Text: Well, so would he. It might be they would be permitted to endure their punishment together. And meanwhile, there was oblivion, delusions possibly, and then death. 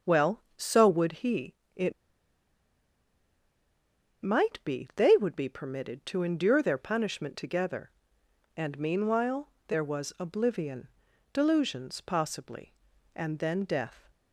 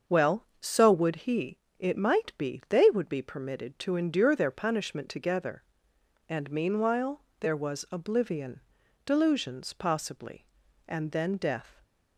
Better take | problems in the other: second | starts louder than the rest; until 1.1 s; 6.5 dB; also in the second // pauses between "It" and "might"; strong; at 1.9 s; 2.3 s long

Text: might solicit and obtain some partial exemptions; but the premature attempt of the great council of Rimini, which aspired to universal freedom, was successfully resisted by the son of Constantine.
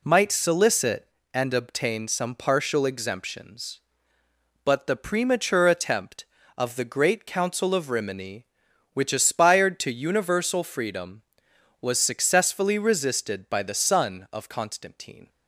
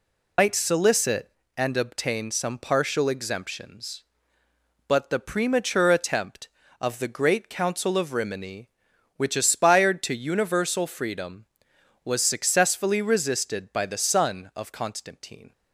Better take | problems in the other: first | loses the start of "might"; at 0.3 s; 105 ms

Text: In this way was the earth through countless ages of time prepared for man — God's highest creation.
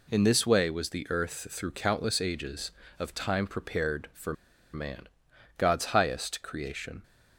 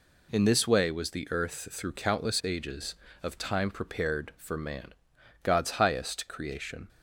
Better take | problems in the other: second | pauses between "for" and "man"; at 4.3 s; 0.41 s long

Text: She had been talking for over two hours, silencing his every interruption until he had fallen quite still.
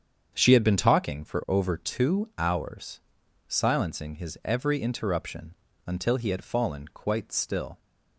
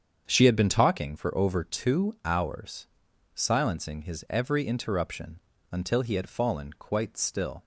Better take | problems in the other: neither | starts louder than the rest; strong; the same in both // pauses between "interruption" and "until"; slight; the same in both

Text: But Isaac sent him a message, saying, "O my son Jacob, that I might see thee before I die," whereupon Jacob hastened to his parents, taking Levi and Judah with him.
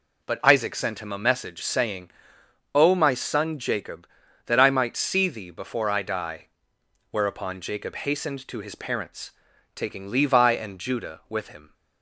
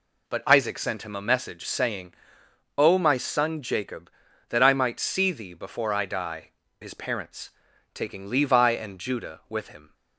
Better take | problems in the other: first | skips "whereupon Jacob hastened to"; at 6.6 s

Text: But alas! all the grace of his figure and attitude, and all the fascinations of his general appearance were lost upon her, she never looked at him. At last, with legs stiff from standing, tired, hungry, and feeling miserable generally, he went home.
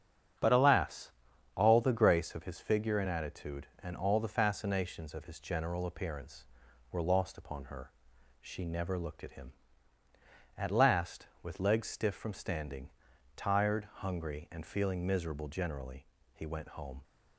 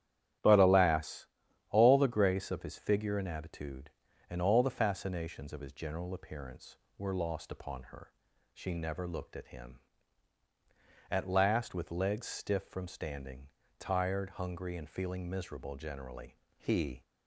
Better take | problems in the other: first | starts louder than the rest; strong; until 1.8 s; 11 dB; strong in the first // stops before "went home"; at 17.0 s

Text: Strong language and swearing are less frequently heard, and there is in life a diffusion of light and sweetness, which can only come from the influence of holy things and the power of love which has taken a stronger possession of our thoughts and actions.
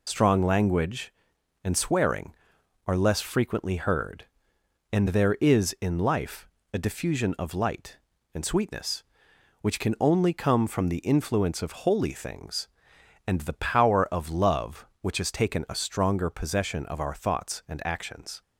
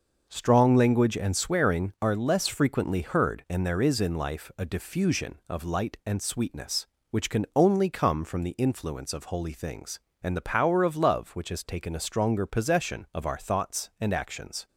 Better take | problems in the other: second | loses the start of "Strong"; at 0.0 s; 45 ms // pauses between "life" and "a"; slight; at 6.4 s; 0.24 s long

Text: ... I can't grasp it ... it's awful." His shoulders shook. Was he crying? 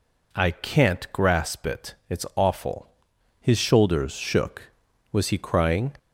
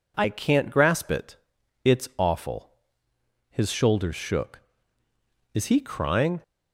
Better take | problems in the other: first | says "Is" for "Was"; at 5.5 s

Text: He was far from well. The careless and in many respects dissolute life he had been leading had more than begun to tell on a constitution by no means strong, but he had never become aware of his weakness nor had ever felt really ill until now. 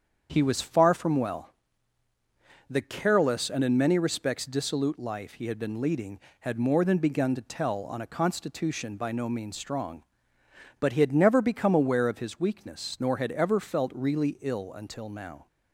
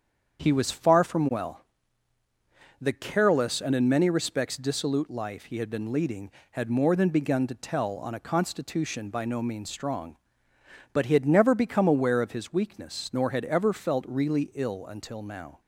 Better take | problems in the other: neither | starts louder than the rest; strong; the same in both

